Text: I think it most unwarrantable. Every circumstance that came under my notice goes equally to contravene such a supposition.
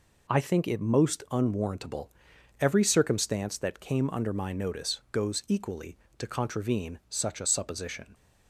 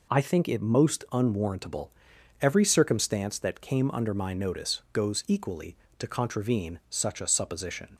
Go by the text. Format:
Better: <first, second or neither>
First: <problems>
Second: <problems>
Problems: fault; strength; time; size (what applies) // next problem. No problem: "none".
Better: neither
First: none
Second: none